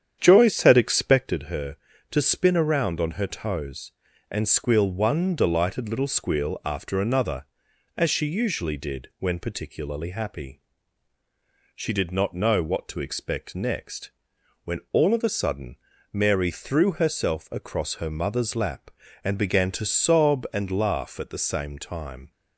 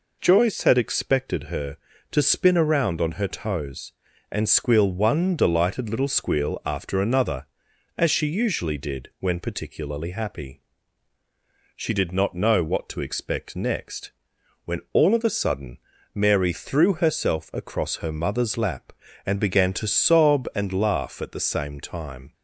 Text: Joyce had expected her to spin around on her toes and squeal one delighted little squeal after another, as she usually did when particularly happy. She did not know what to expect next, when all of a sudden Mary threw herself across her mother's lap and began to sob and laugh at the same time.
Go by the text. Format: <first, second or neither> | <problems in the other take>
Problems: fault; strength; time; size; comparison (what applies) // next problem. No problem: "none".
second | starts louder than the rest; strong; until 1.4 s; 9 dB // pauses between "sudden" and "Mary"; slight; at 15.7 s; 0.34 s long; slight in the second